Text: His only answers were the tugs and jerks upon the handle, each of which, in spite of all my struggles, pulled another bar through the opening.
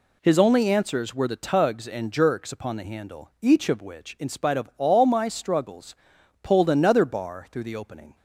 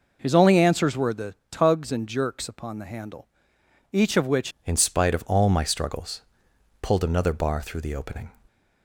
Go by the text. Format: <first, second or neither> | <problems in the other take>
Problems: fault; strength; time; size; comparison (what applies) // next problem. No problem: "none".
first | pauses between "the" and "tugs"; slight; at 1.3 s; 0.16 s long // changes voice at "in"; from 4.6 s on; 3.7 s long